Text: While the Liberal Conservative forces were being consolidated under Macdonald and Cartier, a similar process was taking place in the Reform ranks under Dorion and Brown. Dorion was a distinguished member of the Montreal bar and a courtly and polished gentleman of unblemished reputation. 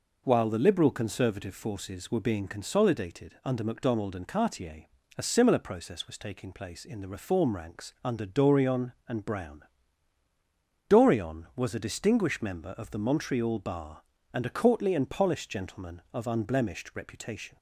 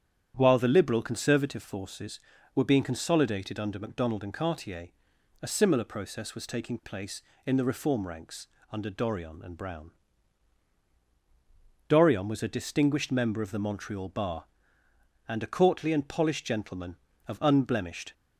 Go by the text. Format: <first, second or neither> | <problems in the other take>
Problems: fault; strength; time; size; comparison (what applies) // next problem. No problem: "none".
first | starts louder than the rest; strong; until 1.3 s; 9.5 dB // pauses between "ranks" and "under"; slight; at 8.4 s; 0.24 s long // stops before "reputation"; at 18.1 s